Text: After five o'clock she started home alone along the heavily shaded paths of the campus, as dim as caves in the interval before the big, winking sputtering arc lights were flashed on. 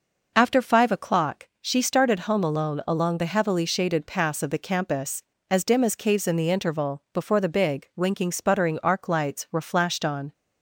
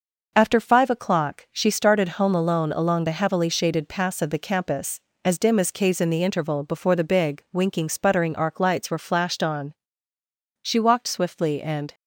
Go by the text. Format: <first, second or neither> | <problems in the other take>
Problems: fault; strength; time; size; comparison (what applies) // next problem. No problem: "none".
first | goes on to say "She walked swiftly and"; from 10.6 s on; 1.3 s long